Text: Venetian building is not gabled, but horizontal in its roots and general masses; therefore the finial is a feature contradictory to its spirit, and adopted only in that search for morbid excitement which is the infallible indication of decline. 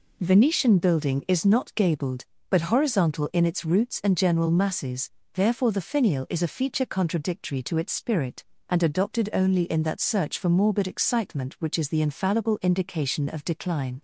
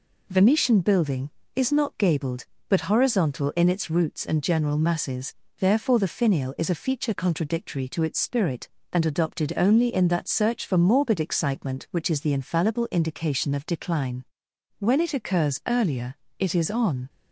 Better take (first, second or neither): first